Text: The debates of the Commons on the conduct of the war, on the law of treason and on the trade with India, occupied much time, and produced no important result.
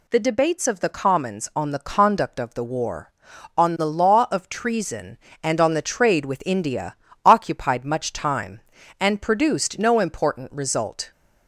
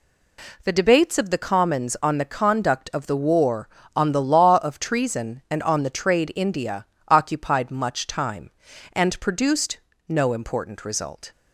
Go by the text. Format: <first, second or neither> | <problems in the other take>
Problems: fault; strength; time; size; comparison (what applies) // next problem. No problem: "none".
first | skips "with"; at 6.3 s // pauses between "produced" and "no"; slight; at 9.7 s; 0.29 s long